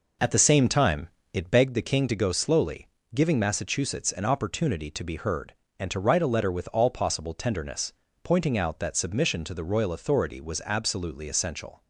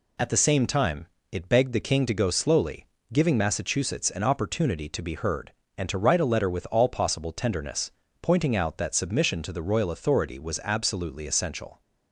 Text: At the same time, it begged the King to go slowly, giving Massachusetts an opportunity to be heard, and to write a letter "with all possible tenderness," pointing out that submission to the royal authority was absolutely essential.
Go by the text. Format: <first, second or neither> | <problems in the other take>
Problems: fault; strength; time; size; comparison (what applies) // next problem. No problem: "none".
second | starts louder than the rest; noticeable; until 1.7 s; 5 dB